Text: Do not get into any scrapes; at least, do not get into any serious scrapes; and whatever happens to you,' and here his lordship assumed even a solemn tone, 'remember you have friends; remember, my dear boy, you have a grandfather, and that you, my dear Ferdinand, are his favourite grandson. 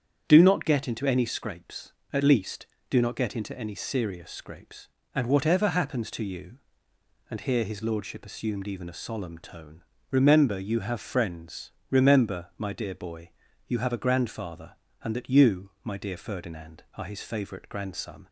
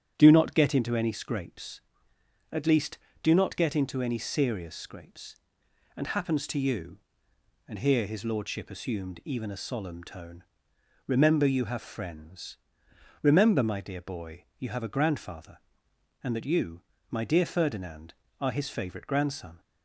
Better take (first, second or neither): first